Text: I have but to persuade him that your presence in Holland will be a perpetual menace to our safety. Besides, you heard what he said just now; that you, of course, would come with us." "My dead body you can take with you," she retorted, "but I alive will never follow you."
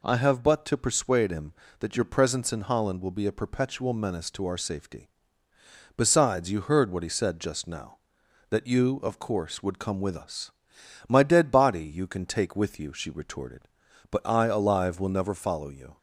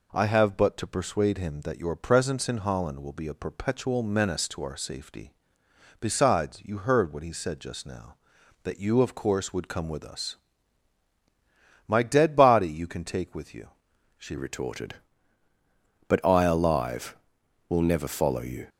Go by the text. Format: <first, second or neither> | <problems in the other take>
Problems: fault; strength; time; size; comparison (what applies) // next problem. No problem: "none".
first | changes voice at "retorted"; from 14.3 s on; 4.3 s long